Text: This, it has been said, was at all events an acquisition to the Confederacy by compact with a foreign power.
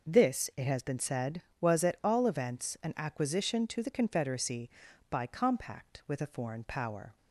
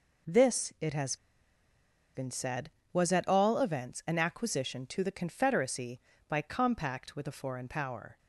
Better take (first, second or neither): first